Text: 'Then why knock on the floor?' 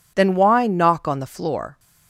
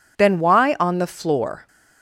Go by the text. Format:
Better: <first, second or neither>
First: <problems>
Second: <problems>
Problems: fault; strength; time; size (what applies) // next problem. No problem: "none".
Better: first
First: none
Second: skips "knock"; at 0.7 s